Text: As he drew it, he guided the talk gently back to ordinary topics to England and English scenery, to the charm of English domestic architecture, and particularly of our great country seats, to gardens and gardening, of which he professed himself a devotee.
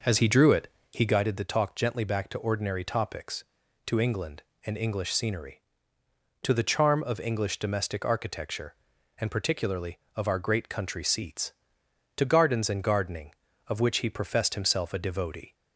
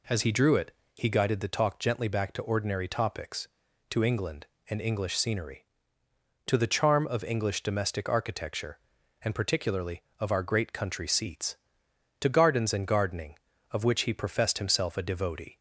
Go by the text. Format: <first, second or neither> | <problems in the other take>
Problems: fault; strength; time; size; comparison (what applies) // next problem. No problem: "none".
second | starts louder than the rest; noticeable; until 1.2 s; 5.5 dB